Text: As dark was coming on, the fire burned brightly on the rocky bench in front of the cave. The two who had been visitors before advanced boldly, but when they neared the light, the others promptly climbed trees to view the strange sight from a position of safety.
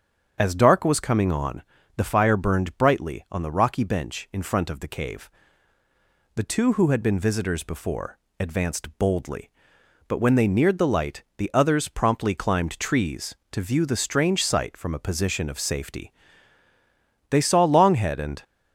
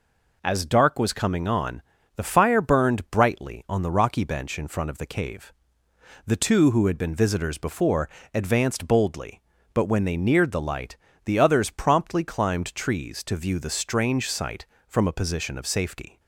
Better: second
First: starts louder than the rest; strong; until 1.3 s; 7 dB // pauses between "before" and "advanced"; slight; at 8.1 s; 0.22 s long // goes on to say "They saw Longhead and"; noticeable; from 17.2 s on; 1.1 s long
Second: pauses between "before" and "advanced"; slight; at 8.0 s; 0.26 s long

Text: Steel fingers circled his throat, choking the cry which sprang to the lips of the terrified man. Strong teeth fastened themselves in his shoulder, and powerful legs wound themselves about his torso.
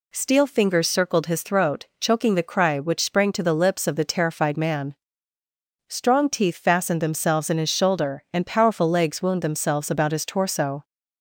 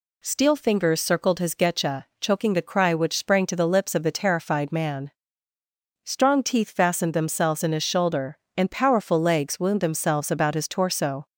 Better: first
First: none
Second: says "getcha" for "throat"; at 1.5 s

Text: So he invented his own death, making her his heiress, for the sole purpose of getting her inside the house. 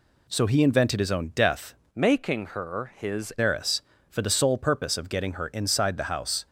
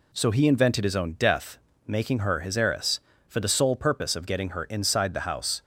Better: second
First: changes voice from "making" to "his"; from 1.9 to 3.3 s; 1.4 s long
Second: none

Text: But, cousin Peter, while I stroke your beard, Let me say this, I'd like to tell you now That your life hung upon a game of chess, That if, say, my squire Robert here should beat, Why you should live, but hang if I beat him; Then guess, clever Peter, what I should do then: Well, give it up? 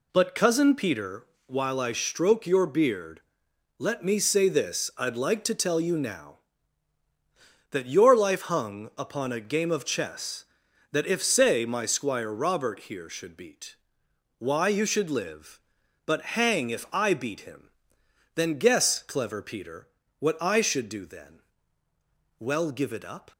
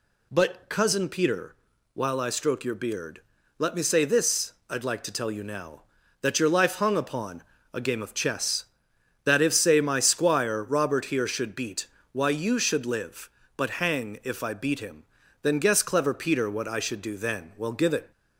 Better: first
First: none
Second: pauses between "upon" and "a"; slight; at 7.4 s; 0.30 s long // stops before "up"; at 18.1 s

